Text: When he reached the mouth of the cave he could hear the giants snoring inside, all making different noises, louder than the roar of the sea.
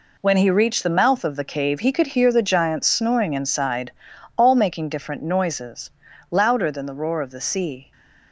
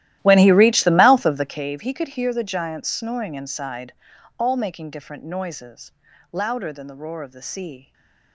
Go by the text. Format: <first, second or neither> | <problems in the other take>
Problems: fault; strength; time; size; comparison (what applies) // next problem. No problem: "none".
first | starts louder than the rest; strong; until 1.7 s; 14.5 dB // stays silent after the last word; slight; from 7.8 s on; 0.5 s long